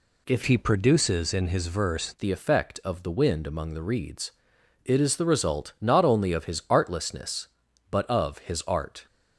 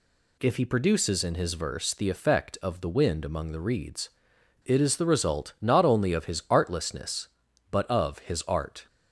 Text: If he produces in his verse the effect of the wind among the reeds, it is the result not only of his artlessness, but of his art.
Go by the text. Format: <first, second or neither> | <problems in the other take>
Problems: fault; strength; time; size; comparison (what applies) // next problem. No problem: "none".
second | changes voice from "he" to "verse"; from 0.4 to 2.1 s; 1.7 s long